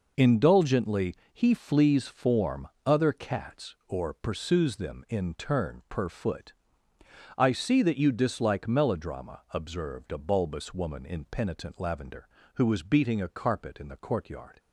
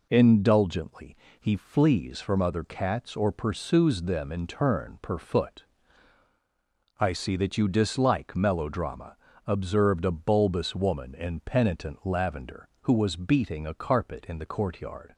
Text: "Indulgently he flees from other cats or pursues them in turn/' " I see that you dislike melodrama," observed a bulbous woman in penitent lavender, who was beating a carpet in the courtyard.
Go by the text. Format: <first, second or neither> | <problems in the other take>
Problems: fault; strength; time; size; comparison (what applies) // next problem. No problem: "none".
second | pauses between "Indulgently" and "he"; slight; at 1.1 s; 0.18 s long; slight in the second // says "form" for "from"; at 2.0 s